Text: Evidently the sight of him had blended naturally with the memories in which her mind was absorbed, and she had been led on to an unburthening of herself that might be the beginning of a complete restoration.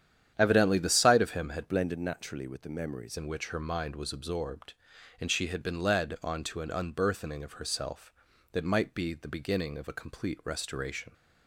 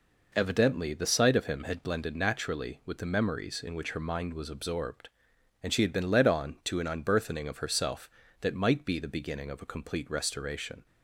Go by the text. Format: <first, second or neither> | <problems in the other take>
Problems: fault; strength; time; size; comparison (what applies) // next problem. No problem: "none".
second | starts louder than the rest; strong; until 1.3 s; 9.5 dB // changes voice from "blended" to "memories"; from 1.6 to 3.1 s; 1.5 s long